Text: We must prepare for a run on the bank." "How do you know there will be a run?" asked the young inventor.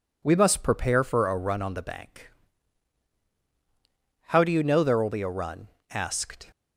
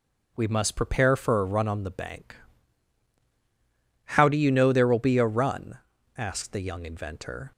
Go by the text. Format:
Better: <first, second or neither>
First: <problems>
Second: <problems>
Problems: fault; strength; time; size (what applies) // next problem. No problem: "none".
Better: second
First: stops before "the young inventor"; at 6.5 s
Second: none